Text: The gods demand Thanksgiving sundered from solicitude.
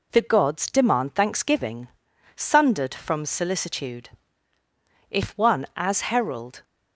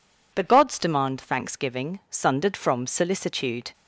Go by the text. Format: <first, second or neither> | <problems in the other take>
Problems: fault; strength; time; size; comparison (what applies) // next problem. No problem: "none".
second | pauses between "Thanksgiving" and "sundered"; noticeable; at 1.8 s; 0.48 s long // goes on to say "If one as herald"; from 5.0 s on; 1.5 s long